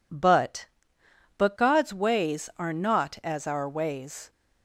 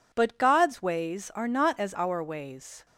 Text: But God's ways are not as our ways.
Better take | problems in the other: second | says "But" twice; at 1.3 s

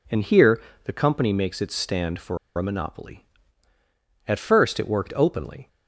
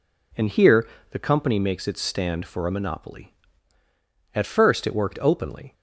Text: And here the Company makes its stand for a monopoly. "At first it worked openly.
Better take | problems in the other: second | pauses between "here" and "the"; slight; at 0.5 s; 0.24 s long; slight in the second // pauses between "for" and "a"; slight; at 2.3 s; 0.20 s long

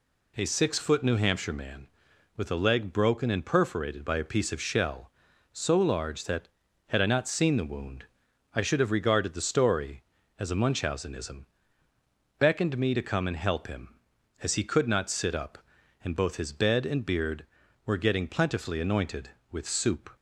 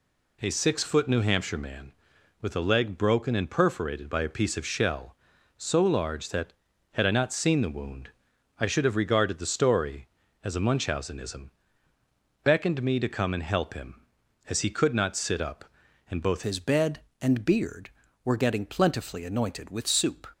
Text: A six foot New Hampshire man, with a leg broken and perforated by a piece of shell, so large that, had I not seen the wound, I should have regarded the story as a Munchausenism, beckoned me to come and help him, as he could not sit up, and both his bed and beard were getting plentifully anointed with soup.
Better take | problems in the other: first | changes voice at "his"; from 16.4 s on; 3.9 s long

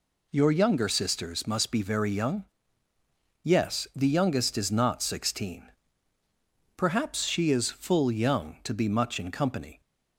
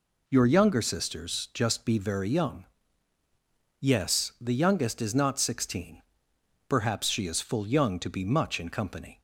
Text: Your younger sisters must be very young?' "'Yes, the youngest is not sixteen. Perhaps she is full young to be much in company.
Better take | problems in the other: first | says "just" for "must"; at 1.5 s

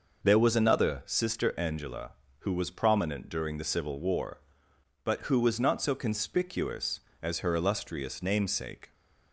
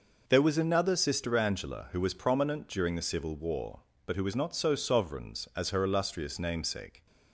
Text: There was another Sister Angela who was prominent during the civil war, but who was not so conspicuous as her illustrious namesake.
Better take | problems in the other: first | says "sovereigns" for "conspicuous"; at 4.7 s

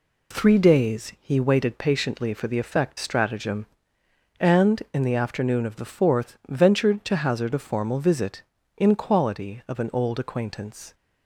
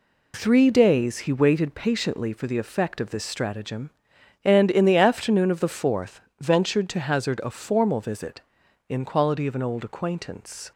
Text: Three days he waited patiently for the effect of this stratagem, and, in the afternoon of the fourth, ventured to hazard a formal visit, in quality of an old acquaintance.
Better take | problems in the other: second | skips "of this"; at 2.9 s

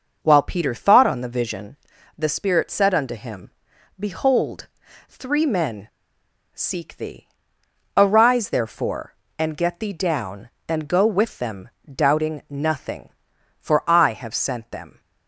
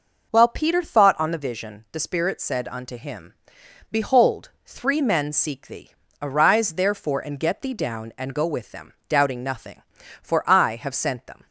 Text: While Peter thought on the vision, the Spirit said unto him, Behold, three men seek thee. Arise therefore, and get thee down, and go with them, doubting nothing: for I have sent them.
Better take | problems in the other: second | starts louder than the rest; noticeable; until 1.2 s; 6 dB // pauses between "men" and "seek"; noticeable; at 5.8 s; 0.65 s long

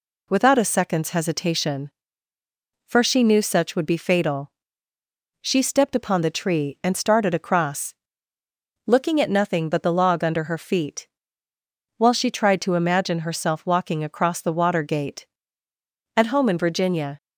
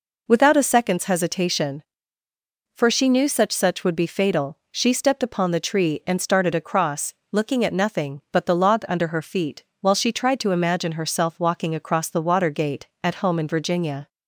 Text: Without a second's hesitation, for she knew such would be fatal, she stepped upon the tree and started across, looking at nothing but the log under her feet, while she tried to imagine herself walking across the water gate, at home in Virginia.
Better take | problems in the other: first | says "such" twice; at 3.5 s

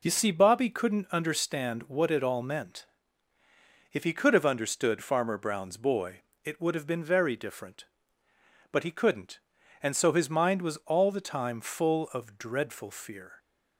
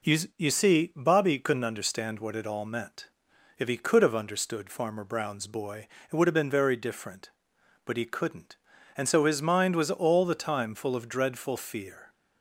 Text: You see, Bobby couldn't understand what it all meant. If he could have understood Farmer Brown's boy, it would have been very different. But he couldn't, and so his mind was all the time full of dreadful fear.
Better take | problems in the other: first | says "You" twice; at 0.3 s

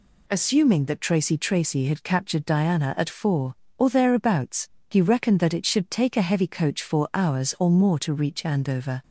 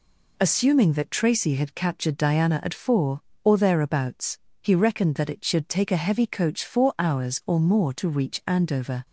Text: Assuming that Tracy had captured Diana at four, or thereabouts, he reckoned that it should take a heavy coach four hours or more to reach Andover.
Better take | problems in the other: second | says "Tracy" twice; at 1.3 s

